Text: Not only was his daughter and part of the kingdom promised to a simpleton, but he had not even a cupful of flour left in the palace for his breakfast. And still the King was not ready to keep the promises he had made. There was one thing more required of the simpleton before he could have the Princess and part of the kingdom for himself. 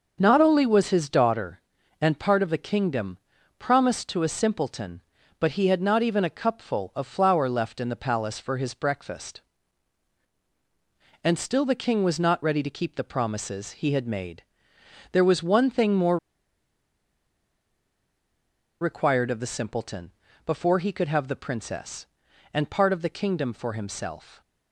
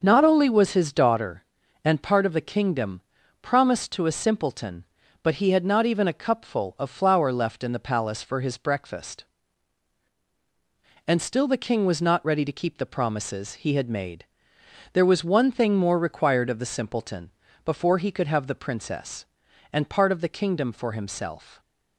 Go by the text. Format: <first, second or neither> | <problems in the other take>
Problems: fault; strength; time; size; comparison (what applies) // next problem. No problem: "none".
second | starts louder than the rest; until 1.2 s; 6.5 dB; also in the second // pauses between "kingdom" and "promised"; at 3.1 s; 0.38 s long; also in the second // pauses between "more" and "required"; strong; at 16.1 s; 2.6 s long // pauses between "simpleton" and "before"; slight; at 20.1 s; 0.36 s long; slight in the second